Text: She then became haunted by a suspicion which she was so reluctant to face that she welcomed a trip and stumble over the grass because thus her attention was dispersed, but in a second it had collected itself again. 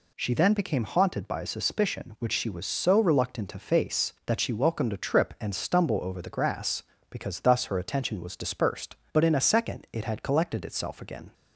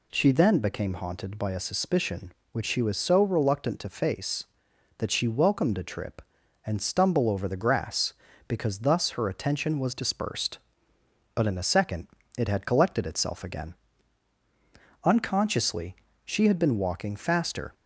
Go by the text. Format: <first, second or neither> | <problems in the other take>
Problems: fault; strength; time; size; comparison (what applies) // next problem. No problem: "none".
first | pauses between "second" and "it"; slight; at 12.0 s; 0.30 s long // goes on to say "Unconsciously she had been walking faster"; strong; from 15.0 s on; 2.6 s long